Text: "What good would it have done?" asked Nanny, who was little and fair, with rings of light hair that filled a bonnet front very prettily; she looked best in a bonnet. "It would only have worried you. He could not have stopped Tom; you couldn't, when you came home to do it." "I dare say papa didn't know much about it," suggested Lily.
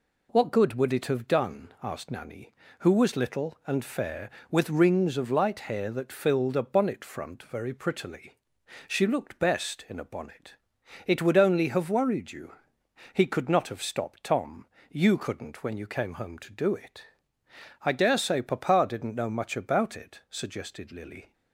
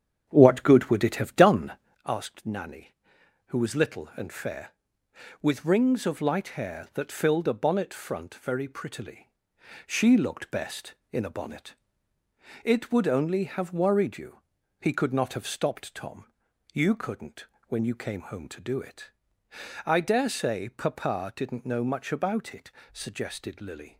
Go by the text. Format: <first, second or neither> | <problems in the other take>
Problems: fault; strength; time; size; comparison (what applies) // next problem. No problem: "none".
first | starts louder than the rest; strong; until 2.0 s; 8.5 dB